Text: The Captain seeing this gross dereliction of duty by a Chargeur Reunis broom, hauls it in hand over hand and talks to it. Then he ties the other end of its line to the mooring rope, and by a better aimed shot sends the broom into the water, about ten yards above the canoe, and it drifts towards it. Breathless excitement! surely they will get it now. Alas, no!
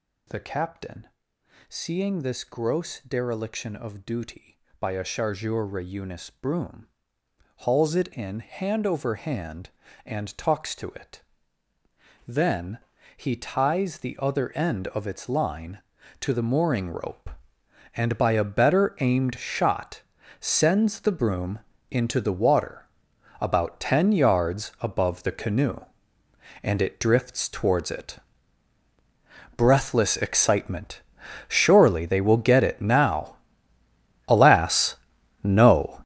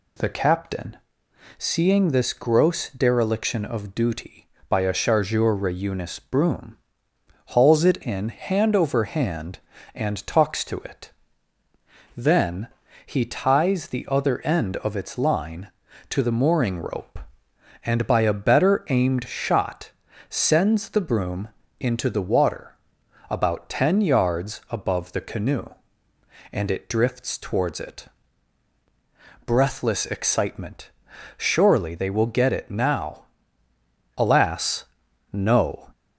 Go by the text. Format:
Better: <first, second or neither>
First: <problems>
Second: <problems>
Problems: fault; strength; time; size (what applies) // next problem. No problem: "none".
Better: second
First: gets louder; strong; throughout; 12 dB // pauses between "Captain" and "seeing"; noticeable; at 1.0 s; 0.64 s long // pauses between "Then" and "he"; at 12.7 s; 0.38 s long // pauses between "shot" and "sends"; at 20.0 s; 0.38 s long // pauses between "broom" and "into"; slight; at 21.5 s; 0.32 s long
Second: pauses between "Captain" and "seeing"; noticeable; at 0.9 s; 0.64 s long // pauses between "Then" and "he"; at 12.6 s; 0.38 s long // pauses between "shot" and "sends"; at 19.9 s; 0.38 s long // pauses between "broom" and "into"; slight; at 21.4 s; 0.32 s long